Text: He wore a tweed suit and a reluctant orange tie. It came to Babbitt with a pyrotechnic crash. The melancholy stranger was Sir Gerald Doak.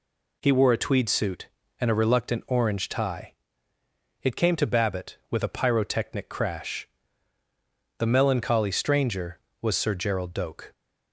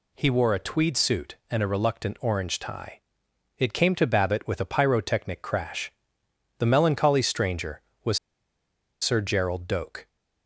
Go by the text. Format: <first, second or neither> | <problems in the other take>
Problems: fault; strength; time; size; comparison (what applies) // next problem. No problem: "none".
first | pauses between "was" and "Sir"; noticeable; at 8.1 s; 0.83 s long